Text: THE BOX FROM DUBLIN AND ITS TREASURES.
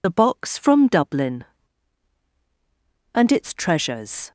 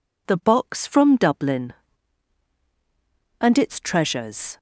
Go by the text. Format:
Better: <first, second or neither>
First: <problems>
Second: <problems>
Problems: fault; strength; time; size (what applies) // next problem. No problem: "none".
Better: second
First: loses the start of "THE"; at 0.0 s; 40 ms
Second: none